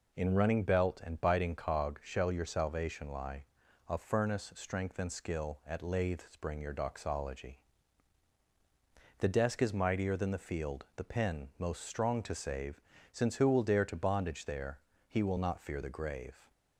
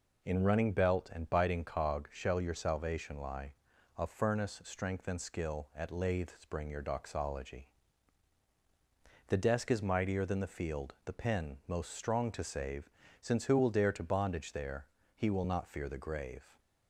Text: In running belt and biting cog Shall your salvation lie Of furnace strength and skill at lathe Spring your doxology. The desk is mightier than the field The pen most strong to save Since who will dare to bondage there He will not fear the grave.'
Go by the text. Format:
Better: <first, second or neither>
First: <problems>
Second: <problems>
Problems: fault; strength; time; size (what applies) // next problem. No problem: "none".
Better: neither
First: pauses between "save" and "Since"; slight; at 12.7 s; 0.32 s long // pauses between "there" and "He"; slight; at 14.8 s; 0.28 s long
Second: pauses between "save" and "Since"; slight; at 12.8 s; 0.32 s long // pauses between "there" and "He"; slight; at 14.8 s; 0.28 s long